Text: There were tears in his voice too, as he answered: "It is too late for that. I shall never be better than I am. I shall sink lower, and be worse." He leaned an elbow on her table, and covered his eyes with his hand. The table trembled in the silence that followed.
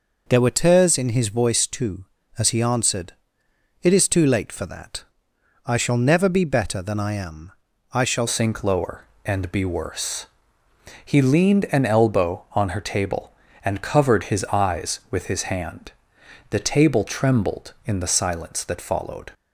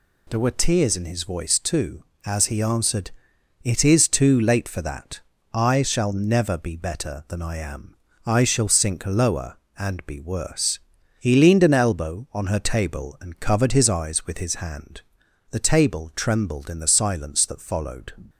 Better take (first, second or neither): second